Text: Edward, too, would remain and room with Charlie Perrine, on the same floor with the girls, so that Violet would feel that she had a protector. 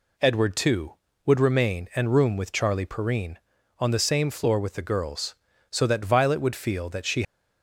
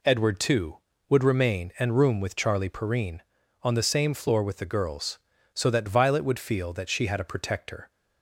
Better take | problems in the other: second | stops before "had a protector"; at 7.2 s

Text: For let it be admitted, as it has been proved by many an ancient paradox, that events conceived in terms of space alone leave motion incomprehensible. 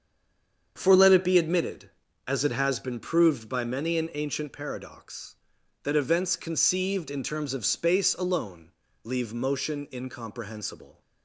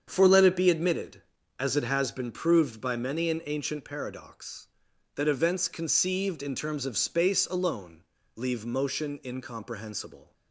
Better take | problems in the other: second | stays silent before the first word; slight; until 0.7 s; 0.7 s long // starts louder than the rest; strong; until 1.7 s; 7.5 dB; strong in the second // pauses between "alone" and "leave"; slight; at 8.7 s; 0.32 s long; slight in the second

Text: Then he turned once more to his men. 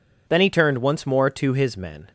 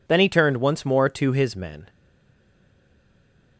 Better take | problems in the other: first | stays silent after the last word; noticeable; from 1.8 s on; 1.7 s long

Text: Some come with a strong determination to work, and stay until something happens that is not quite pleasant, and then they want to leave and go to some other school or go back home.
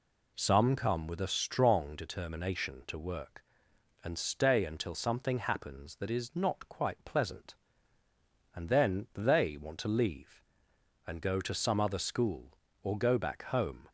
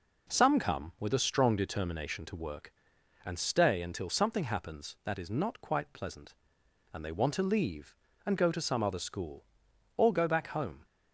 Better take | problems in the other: first | skips "then"; at 7.0 s

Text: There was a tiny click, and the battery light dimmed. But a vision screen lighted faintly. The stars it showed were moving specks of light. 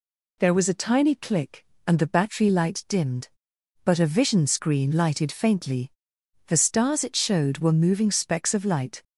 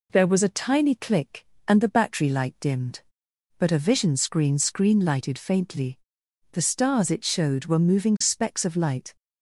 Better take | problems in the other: first | says "screen" twice; at 4.5 s

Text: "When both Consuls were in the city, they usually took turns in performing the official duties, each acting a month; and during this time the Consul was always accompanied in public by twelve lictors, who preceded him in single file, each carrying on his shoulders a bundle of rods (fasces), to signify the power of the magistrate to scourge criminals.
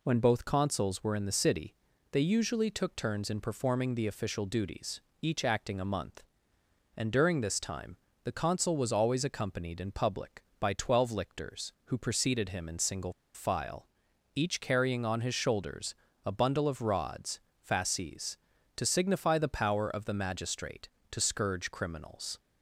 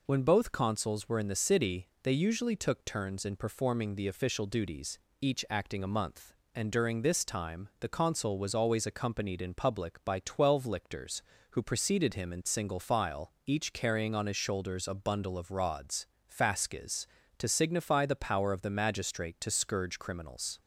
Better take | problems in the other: second | pauses between "time" and "the"; slight; at 7.9 s; 0.26 s long // pauses between "single" and "file"; slight; at 13.1 s; 0.21 s long // pauses between "shoulders" and "a"; slight; at 15.9 s; 0.32 s long

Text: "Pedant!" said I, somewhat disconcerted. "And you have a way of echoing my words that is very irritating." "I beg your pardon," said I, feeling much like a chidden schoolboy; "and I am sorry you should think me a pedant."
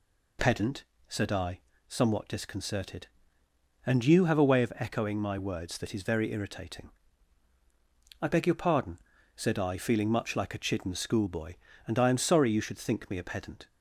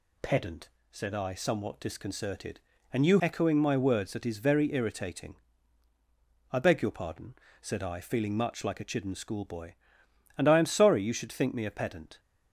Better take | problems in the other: first | skips "have a way of"; at 3.1 s

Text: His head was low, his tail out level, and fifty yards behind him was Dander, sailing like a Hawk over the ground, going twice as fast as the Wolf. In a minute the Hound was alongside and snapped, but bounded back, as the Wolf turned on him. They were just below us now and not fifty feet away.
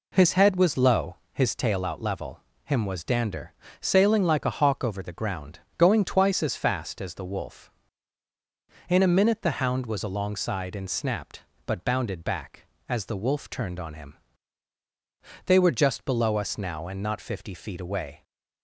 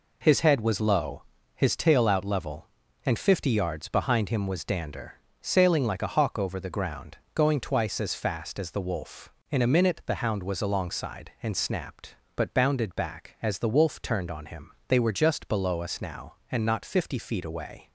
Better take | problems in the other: second | skips "and fifty yards behind"; at 2.5 s

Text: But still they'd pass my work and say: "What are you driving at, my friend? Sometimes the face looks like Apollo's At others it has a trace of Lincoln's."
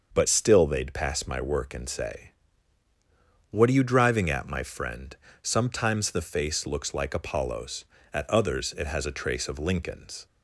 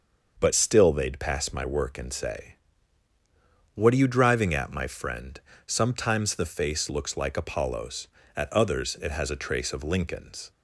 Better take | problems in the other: neither | starts louder than the rest; the same in both

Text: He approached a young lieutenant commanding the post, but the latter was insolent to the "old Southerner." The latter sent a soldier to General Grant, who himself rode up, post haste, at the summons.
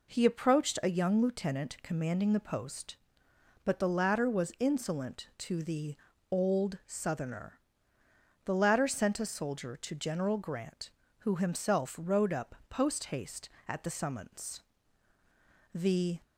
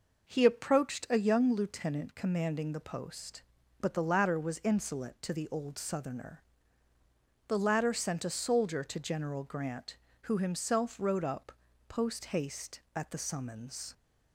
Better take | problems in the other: second | pauses between "the" and "old"; slight; at 5.9 s; 0.36 s long // goes on to say "The"; slight; from 15.7 s on; 0.48 s long

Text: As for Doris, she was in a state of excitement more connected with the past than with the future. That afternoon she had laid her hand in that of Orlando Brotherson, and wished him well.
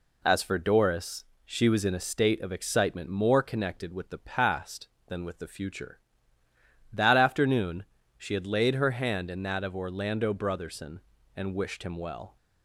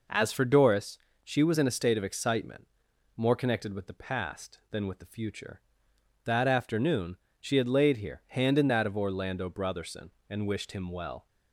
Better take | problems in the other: first | pauses between "excitement" and "more"; noticeable; at 2.6 s; 0.50 s long // pauses between "afternoon" and "she"; slight; at 7.1 s; 0.24 s long; slight in the first // says "here" for "her"; at 7.9 s

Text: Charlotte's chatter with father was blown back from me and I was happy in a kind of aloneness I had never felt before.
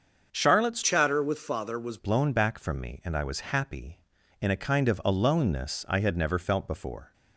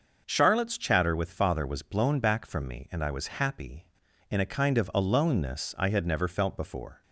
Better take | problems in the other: second | starts louder than the rest; until 1.3 s; 7 dB; also in the second // changes voice from "chatter" to "was"; from 0.8 to 1.9 s; 1.1 s long

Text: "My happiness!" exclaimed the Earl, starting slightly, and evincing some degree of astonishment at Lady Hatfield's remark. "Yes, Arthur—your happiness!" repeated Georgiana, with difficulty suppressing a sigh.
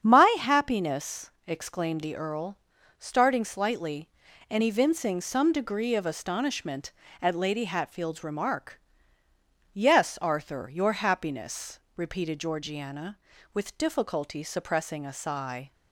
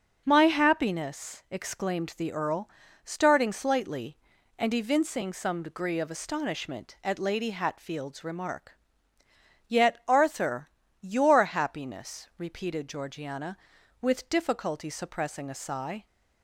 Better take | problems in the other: first | starts louder than the rest; strong; until 1.2 s; 7 dB; strong in the first // says "Yet" for "Yes"; at 9.6 s

